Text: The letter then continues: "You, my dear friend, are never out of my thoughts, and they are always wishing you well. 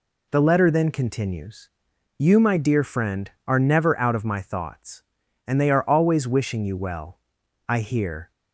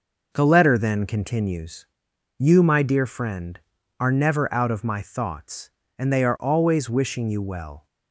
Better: second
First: goes on to say "I hear"; noticeable; from 7.6 s on; 0.62 s long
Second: none

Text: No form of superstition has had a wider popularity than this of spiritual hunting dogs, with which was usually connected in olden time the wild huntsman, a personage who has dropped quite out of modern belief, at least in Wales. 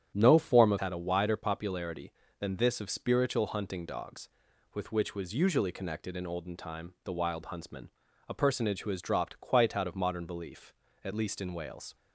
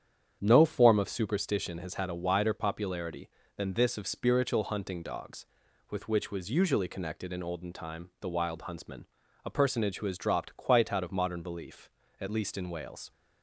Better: second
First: starts louder than the rest; strong; until 1.1 s; 9 dB // skips "superstition has"; at 0.7 s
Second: starts louder than the rest; strong; until 1.4 s; 8.5 dB

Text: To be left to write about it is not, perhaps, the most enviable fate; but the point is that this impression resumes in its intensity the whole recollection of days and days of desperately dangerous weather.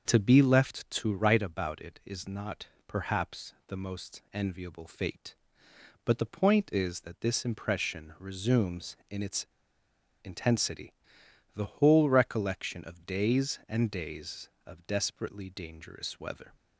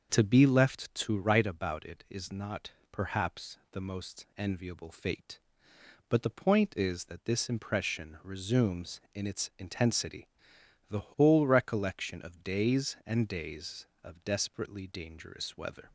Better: second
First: starts louder than the rest; until 1.0 s; 6.5 dB // pauses between "its" and "intensity"; noticeable; at 9.4 s; 0.75 s long // pauses between "intensity" and "the"; noticeable; at 10.9 s; 0.62 s long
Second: starts louder than the rest; until 1.1 s; 6.5 dB // pauses between "intensity" and "the"; noticeable; at 10.2 s; 0.62 s long

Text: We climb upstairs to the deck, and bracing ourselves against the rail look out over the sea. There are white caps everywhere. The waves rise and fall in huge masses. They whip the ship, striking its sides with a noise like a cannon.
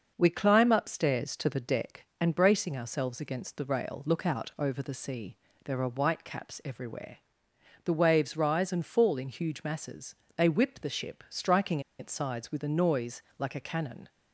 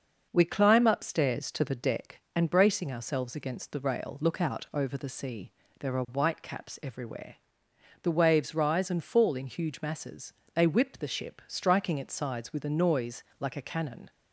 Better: second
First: starts louder than the rest; noticeable; until 1.1 s; 6 dB // pauses between "striking" and "its"; slight; at 11.7 s; 0.19 s long // pauses between "noise" and "like"; slight; at 13.2 s; 0.16 s long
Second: starts louder than the rest; noticeable; until 1.3 s; 6 dB // pauses between "noise" and "like"; slight; at 13.2 s; 0.16 s long

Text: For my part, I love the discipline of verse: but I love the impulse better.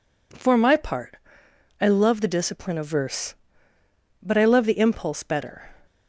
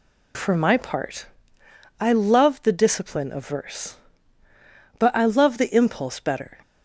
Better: neither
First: none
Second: none

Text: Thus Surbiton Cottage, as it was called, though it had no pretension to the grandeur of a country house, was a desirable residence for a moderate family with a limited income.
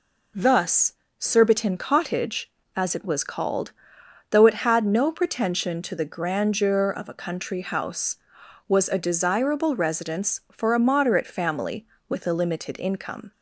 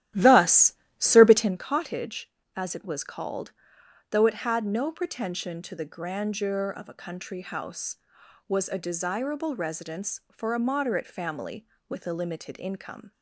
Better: first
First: pauses between "Thus" and "Surbiton"; slight; at 0.9 s; 0.26 s long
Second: starts louder than the rest; strong; until 1.6 s; 13 dB // pauses between "Thus" and "Surbiton"; slight; at 0.7 s; 0.26 s long

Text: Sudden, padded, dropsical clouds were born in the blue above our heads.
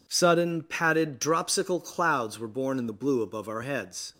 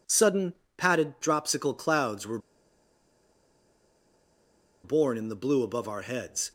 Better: first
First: none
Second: pauses between "were" and "born"; strong; at 2.3 s; 2.4 s long

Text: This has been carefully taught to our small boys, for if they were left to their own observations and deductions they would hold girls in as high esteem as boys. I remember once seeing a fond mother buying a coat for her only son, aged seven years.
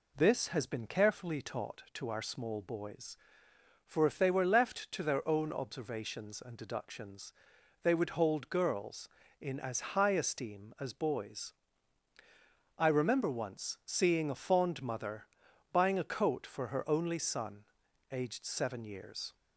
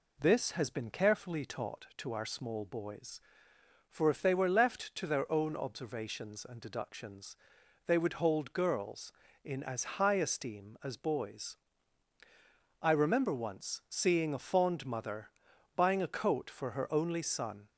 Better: first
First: pauses between "deductions" and "they"; noticeable; at 7.3 s; 0.50 s long // pauses between "mother" and "buying"; noticeable; at 15.2 s; 0.46 s long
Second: pauses between "deductions" and "they"; noticeable; at 7.3 s; 0.50 s long // pauses between "mother" and "buying"; noticeable; at 15.3 s; 0.46 s long // stops before "aged seven years"; at 17.6 s

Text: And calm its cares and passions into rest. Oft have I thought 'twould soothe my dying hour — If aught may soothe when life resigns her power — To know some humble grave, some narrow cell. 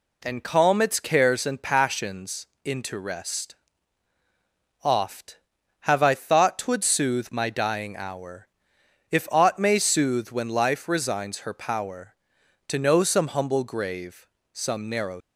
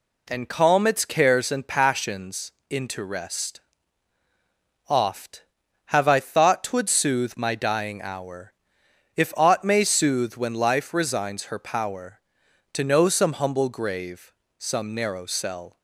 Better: second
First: pauses between "passions" and "into"; slight; at 2.4 s; 0.16 s long // stops before "cell"; at 15.1 s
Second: pauses between "passions" and "into"; slight; at 2.5 s; 0.16 s long

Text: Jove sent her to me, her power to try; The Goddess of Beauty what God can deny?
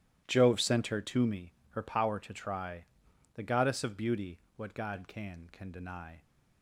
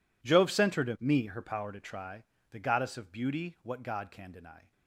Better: second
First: starts louder than the rest; strong; until 1.2 s; 12.5 dB // pauses between "Beauty" and "what"; slight; at 4.3 s; 0.18 s long // says "can" twice; at 5.5 s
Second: none

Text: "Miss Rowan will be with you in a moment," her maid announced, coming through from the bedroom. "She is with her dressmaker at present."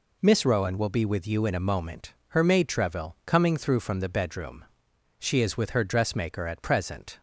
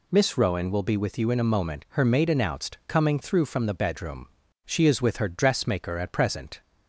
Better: second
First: says "treville" for "announced"; at 2.6 s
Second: none

